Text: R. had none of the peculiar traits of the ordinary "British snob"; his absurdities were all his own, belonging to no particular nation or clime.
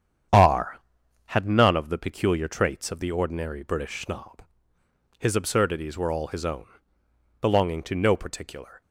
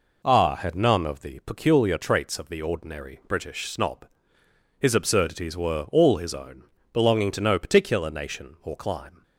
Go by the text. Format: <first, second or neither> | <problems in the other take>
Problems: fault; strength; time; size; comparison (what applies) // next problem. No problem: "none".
second | starts louder than the rest; strong; until 1.7 s; 8.5 dB // stops before "nation or clime"; at 8.8 s